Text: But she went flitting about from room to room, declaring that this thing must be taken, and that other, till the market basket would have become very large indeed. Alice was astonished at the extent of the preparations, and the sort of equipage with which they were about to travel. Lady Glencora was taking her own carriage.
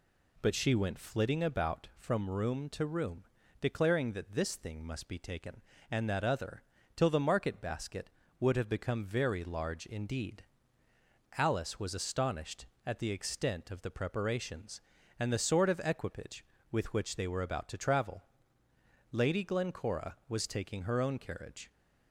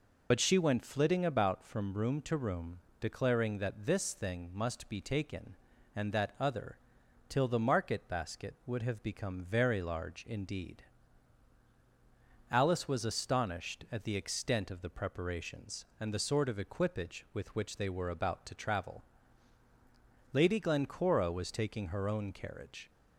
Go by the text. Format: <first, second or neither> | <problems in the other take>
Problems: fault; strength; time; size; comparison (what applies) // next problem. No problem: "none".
first | loses the start of "But"; at 0.3 s; 55 ms